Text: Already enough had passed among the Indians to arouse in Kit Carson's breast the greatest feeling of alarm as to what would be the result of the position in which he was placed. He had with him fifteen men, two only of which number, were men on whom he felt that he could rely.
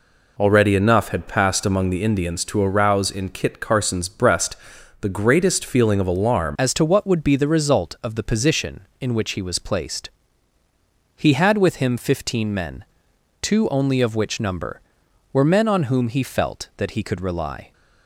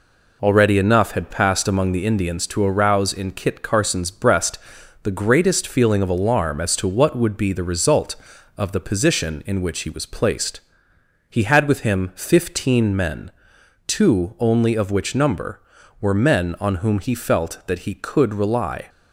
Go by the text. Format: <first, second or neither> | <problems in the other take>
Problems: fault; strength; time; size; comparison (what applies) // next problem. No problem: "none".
second | pauses between "breast" and "the"; noticeable; at 4.5 s; 0.46 s long; noticeable in the second // changes voice at "as"; from 6.5 s on; 11.2 s long